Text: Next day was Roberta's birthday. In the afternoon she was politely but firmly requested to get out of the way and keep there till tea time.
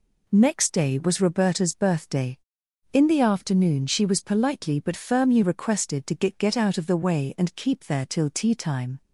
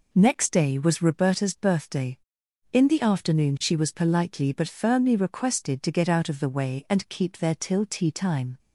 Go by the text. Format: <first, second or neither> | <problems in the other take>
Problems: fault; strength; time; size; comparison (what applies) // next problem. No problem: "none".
second | says "get" twice; at 6.3 s